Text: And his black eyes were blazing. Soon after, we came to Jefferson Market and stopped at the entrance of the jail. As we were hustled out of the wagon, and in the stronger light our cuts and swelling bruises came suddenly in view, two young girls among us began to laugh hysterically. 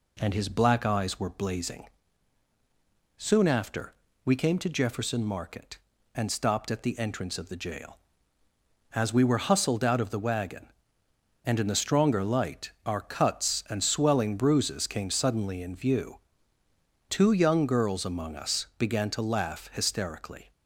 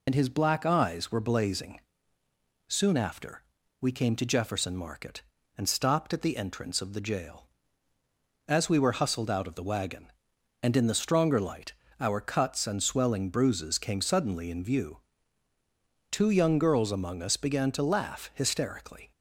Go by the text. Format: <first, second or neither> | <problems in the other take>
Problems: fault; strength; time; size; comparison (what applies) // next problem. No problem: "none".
first | loses the start of "And"; at 0.0 s; 65 ms // pauses between "light" and "our"; slight; at 11.7 s; 0.26 s long